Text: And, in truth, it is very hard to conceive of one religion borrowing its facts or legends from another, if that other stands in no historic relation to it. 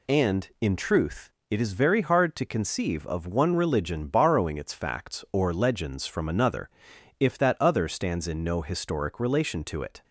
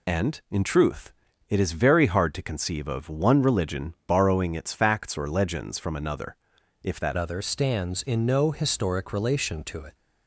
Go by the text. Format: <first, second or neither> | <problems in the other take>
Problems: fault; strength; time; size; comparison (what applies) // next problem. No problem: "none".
first | changes voice at "other"; from 7.1 s on; 2.8 s long